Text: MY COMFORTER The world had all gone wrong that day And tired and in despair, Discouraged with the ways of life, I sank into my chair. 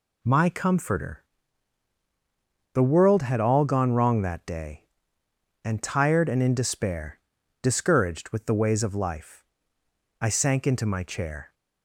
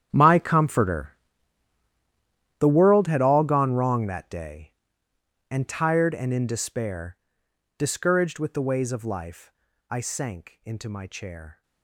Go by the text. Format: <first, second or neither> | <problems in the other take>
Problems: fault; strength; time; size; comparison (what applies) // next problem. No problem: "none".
first | gets quieter; strong; throughout; 17 dB // pauses between "COMFORTER" and "The"; strong; at 1.1 s; 1.4 s long; strong in the first